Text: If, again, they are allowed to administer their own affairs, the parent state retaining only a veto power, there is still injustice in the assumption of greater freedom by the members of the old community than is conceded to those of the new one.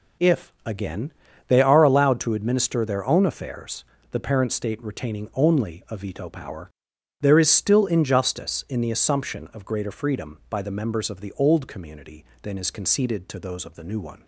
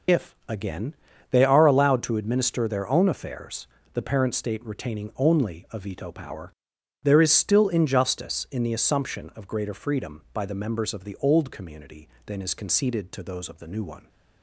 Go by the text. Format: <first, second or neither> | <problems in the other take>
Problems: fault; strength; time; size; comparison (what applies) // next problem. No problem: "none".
first | loses the start of "If"; at 0.0 s; 55 ms